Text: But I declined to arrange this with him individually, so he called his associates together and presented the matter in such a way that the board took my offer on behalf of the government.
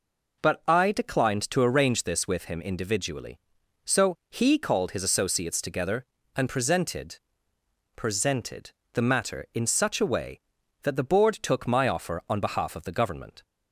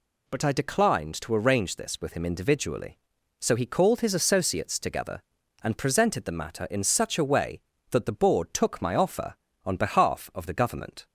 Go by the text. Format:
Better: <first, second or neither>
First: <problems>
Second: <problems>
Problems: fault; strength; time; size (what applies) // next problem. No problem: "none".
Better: second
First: pauses between "so" and "he"; slight; at 4.1 s; 0.16 s long // says "presented" twice; at 7.9 s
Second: none